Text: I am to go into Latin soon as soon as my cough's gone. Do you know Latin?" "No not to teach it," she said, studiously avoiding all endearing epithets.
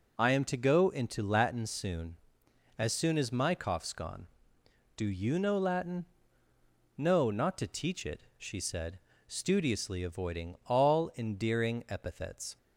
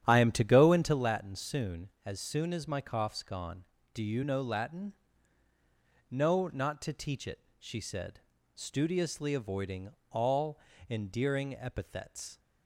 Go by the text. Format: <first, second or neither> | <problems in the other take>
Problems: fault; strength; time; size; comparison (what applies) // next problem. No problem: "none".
first | starts louder than the rest; strong; until 1.0 s; 10 dB // pauses between "avoiding" and "all"; slight; at 9.9 s; 0.20 s long // pauses between "all" and "endearing"; slight; at 10.5 s; 0.30 s long